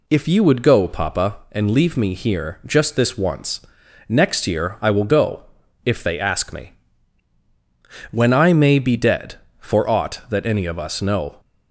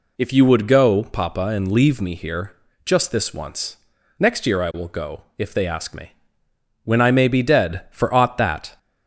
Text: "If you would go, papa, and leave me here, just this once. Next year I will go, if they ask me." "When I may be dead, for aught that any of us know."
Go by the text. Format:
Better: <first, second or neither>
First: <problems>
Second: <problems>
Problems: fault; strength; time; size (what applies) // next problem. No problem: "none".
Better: first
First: none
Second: stops before "any of us know"; at 8.7 s